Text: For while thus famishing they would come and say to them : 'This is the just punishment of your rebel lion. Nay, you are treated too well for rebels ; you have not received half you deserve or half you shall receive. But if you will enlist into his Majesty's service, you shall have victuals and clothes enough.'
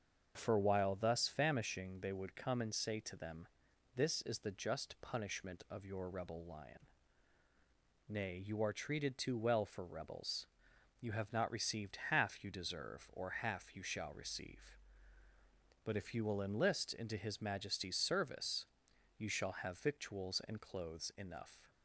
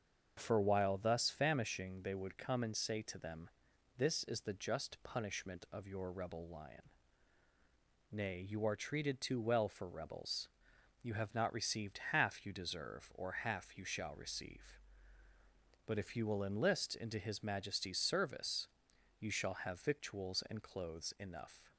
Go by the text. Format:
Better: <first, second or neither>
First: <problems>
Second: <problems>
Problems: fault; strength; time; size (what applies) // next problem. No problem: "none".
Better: neither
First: starts louder than the rest; until 1.3 s; 7 dB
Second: starts louder than the rest; until 1.3 s; 7 dB